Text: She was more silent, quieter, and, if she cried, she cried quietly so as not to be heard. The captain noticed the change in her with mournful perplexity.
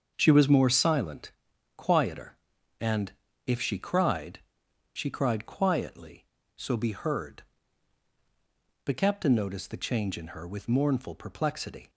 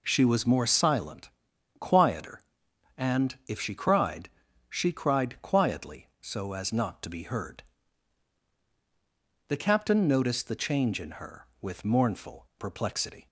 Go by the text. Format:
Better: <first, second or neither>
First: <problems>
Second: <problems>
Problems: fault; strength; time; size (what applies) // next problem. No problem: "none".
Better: second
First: starts louder than the rest; until 1.1 s; 6.5 dB // skips "as not to"; at 6.7 s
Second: none